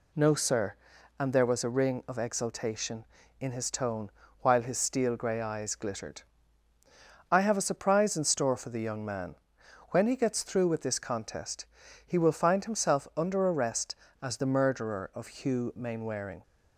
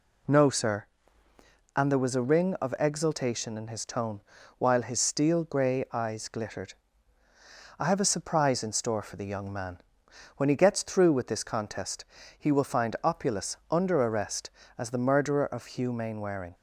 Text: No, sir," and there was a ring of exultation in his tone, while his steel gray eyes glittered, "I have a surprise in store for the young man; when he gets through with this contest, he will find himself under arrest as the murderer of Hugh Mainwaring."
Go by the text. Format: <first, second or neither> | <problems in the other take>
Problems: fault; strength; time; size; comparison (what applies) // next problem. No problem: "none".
first | says "opulus" for "himself"; at 13.0 s